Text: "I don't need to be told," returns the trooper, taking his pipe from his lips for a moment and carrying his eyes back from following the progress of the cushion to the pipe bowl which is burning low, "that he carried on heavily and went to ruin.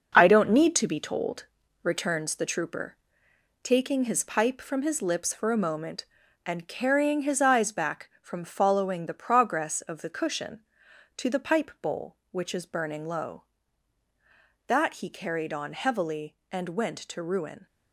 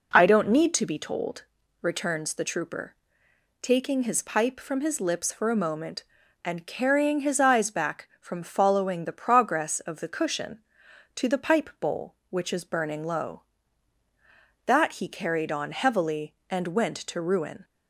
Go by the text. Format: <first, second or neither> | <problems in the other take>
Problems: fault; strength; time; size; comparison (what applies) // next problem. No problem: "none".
second | gets quieter; strong; throughout; 7 dB